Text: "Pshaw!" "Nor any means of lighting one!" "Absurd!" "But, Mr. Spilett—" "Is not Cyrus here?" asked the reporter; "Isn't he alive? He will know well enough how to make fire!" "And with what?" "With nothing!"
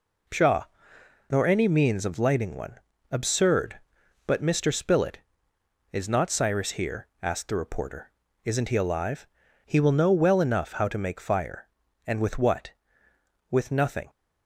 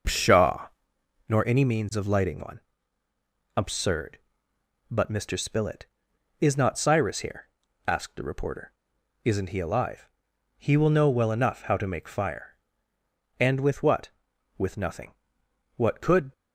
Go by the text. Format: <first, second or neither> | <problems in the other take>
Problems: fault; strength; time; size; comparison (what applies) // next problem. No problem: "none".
first | goes on to say "What could"; from 15.7 s on; 0.56 s long